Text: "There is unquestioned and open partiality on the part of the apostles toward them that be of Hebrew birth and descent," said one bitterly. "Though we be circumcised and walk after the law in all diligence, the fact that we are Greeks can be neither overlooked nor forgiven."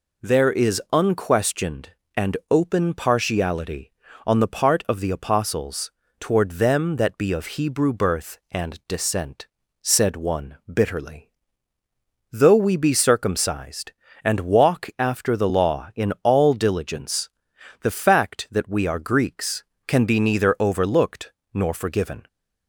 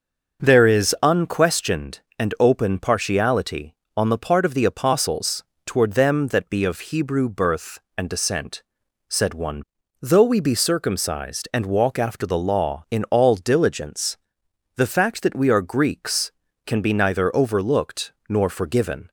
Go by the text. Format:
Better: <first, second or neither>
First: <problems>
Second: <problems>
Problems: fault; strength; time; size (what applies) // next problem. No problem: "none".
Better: first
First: pauses between "apostles" and "toward"; slight; at 5.9 s; 0.28 s long // pauses between "overlooked" and "nor"; slight; at 21.3 s; 0.22 s long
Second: starts louder than the rest; noticeable; until 1.4 s; 6 dB // pauses between "apostles" and "toward"; slight; at 5.4 s; 0.24 s long // skips "bitterly"; at 9.8 s // pauses between "overlooked" and "nor"; slight; at 18.1 s; 0.16 s long